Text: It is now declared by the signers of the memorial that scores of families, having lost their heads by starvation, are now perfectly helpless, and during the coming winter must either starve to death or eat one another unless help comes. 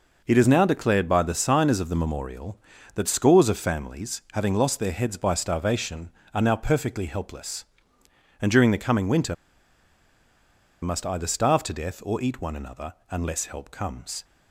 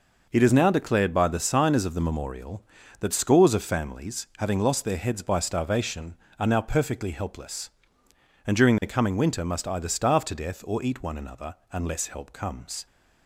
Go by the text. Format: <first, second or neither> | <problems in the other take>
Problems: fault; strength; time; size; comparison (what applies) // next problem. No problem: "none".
second | pauses between "winter" and "must"; strong; at 9.3 s; 1.4 s long // pauses between "another" and "unless"; slight; at 12.9 s; 0.18 s long; slight in the second